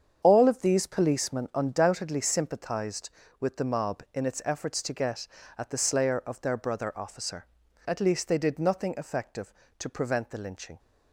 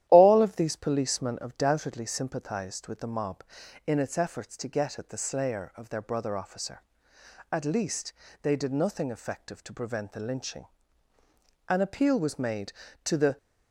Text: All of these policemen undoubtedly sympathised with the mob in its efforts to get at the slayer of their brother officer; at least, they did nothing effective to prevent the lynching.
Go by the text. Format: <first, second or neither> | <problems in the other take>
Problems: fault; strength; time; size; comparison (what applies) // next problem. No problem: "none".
first | starts louder than the rest; strong; until 1.0 s; 12 dB; strong in the first // goes on to say "An appeal was made to the"; strong; from 11.6 s on; 1.6 s long